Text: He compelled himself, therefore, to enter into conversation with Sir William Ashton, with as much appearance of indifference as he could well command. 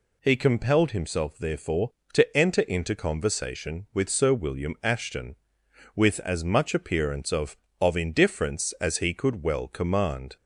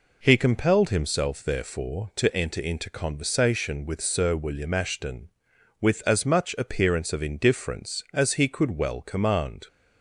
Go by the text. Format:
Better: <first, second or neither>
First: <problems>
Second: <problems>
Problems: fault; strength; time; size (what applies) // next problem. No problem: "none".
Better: second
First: says "of" twice; at 7.7 s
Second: none